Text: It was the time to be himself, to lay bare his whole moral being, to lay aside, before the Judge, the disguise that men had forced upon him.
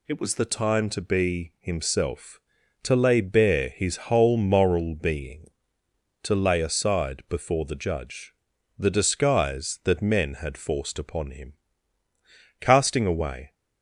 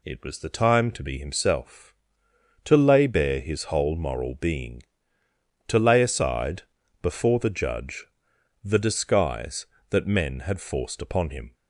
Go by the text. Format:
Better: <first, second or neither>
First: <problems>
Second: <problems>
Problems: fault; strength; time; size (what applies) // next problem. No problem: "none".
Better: second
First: goes on to say "Casting away"; noticeable; from 12.5 s on; 0.94 s long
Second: none